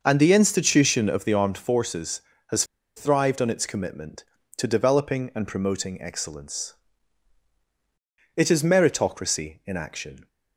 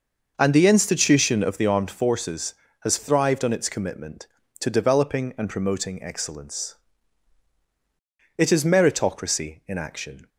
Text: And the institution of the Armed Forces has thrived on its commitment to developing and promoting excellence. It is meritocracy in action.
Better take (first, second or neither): second